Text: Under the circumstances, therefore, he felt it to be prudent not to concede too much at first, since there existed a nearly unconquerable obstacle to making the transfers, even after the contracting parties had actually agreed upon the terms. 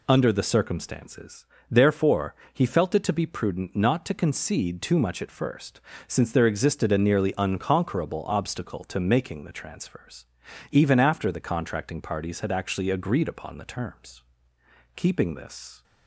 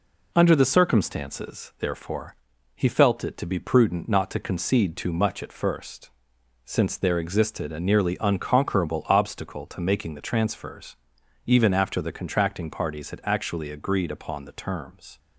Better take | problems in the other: second | goes on to say "Keeping this"; noticeable; from 14.9 s on; 0.88 s long

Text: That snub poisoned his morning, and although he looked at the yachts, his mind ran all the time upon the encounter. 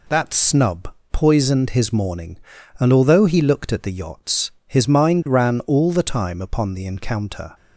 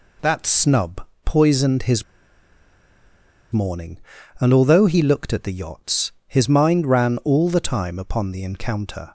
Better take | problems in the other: first | pauses between "snub" and "poisoned"; slight; at 1.0 s; 0.18 s long; slight in the first // pauses between "his" and "morning"; strong; at 2.0 s; 1.4 s long

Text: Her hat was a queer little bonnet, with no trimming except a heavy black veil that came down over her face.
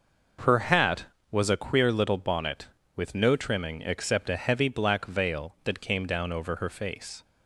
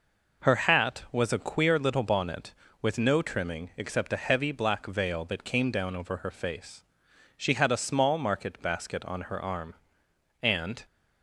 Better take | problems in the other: first | goes on to say "She had a small market basket on her arm and"; strong; from 7.3 s on; 3.4 s long

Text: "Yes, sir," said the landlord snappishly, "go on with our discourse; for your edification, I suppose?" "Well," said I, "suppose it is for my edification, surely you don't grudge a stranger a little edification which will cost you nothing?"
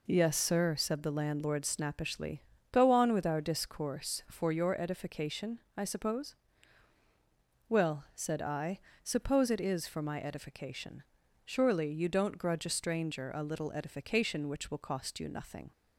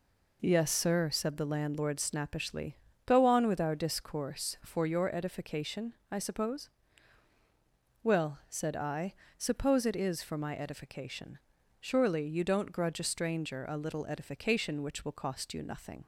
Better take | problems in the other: neither | none

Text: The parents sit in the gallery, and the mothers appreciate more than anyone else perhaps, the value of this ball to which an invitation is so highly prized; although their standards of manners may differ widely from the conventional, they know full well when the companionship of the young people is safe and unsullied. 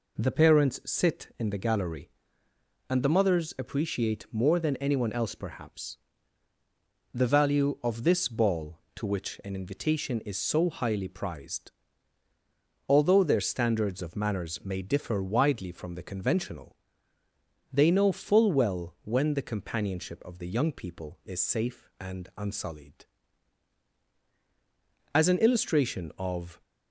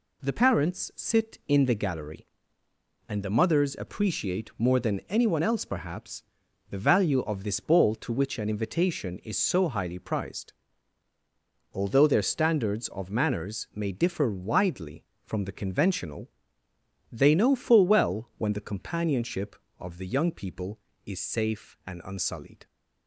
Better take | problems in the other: second | goes on to say "As an illustration of"; from 25.1 s on; 1.4 s long

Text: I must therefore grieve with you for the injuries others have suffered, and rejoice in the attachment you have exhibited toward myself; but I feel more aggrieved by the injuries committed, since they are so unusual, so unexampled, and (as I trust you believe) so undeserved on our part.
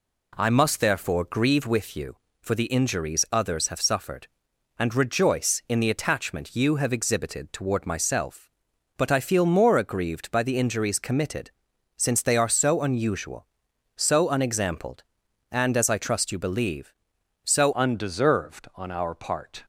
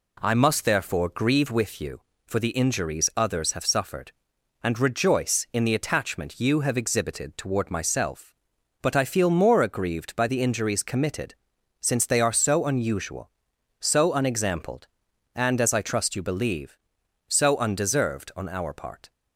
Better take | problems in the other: second | changes voice at "undeserved"; from 17.7 s on; 1.9 s long

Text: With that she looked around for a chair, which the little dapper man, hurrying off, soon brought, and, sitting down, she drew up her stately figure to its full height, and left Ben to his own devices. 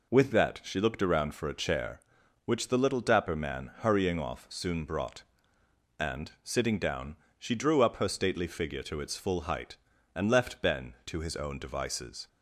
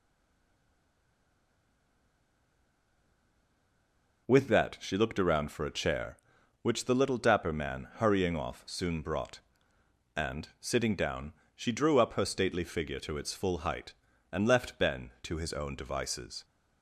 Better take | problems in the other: first | stays silent before the first word; strong; until 4.2 s; 4.2 s long

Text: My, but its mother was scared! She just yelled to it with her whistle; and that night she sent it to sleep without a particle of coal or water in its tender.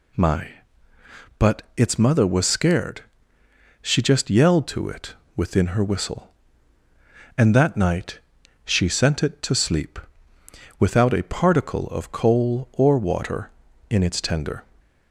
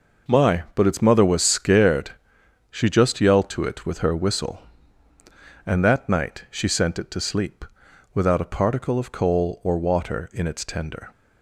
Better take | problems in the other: second | pauses between "but" and "its"; slight; at 1.6 s; 0.16 s long // says "within" for "with"; at 5.3 s // pauses between "night" and "she"; noticeable; at 8.1 s; 0.46 s long // pauses between "sleep" and "without"; noticeable; at 9.9 s; 0.80 s long; noticeable in the second

